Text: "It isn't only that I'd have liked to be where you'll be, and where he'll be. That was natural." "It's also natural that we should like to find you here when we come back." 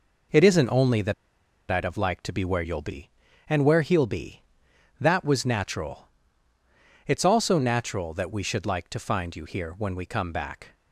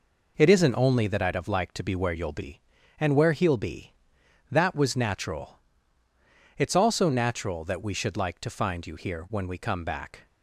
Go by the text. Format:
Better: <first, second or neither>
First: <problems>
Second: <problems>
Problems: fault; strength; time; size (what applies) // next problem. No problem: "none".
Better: second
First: pauses between "that" and "I'd"; noticeable; at 1.1 s; 0.57 s long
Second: none